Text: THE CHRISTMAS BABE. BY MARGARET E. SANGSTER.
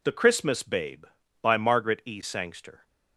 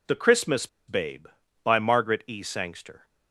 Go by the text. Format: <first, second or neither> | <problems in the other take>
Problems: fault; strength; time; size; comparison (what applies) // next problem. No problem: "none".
first | pauses between "CHRISTMAS" and "BABE"; slight; at 0.6 s; 0.20 s long